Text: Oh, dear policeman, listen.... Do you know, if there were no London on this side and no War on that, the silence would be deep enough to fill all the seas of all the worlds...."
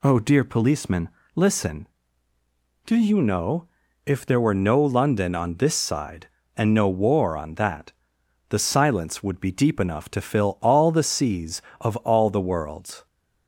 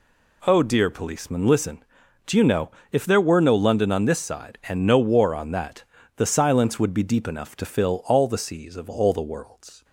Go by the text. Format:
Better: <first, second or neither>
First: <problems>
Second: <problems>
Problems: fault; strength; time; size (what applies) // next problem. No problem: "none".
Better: neither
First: none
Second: none